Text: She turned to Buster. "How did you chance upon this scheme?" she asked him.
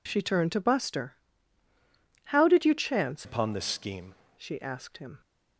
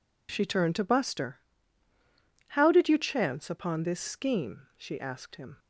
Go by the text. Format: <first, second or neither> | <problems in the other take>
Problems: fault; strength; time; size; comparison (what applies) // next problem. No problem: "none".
second | changes voice from "upon" to "scheme"; from 3.2 to 4.1 s; 0.9 s long